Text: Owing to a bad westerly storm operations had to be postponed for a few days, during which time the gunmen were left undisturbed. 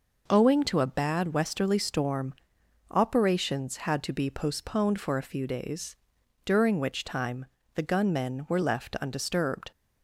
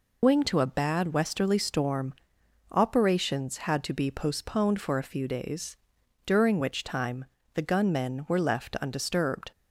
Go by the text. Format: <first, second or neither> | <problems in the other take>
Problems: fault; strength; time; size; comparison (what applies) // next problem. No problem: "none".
first | loses the start of "Owing"; at 0.2 s; 175 ms // pauses between "storm" and "operations"; noticeable; at 2.1 s; 0.56 s long; noticeable in the first // pauses between "time" and "the"; slight; at 7.2 s; 0.30 s long; slight in the first